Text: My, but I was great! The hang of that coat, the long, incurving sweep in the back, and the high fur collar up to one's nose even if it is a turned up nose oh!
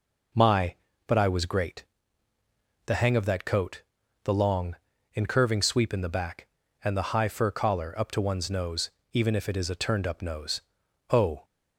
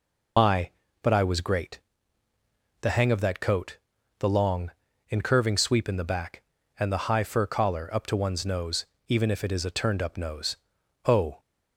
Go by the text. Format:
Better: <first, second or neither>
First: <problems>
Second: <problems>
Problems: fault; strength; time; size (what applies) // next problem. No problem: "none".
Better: first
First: pauses between "nose" and "even"; slight; at 8.9 s; 0.22 s long // pauses between "nose" and "oh"; noticeable; at 10.6 s; 0.50 s long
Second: loses the start of "My"; at 0.3 s; 70 ms // pauses between "nose" and "even"; slight; at 8.8 s; 0.22 s long // pauses between "nose" and "oh"; noticeable; at 10.5 s; 0.50 s long